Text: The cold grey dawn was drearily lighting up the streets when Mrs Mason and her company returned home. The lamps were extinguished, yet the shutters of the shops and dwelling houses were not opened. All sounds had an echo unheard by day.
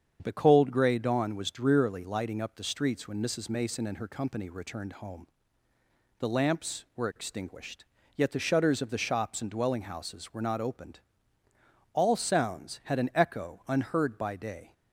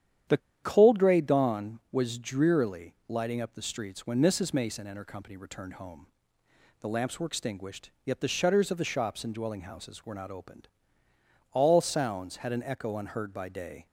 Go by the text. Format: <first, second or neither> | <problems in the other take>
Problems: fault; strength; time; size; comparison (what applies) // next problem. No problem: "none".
first | starts louder than the rest; strong; until 1.5 s; 9.5 dB; strong in the first // pauses between "The" and "cold"; slight; at 0.3 s; 0.24 s long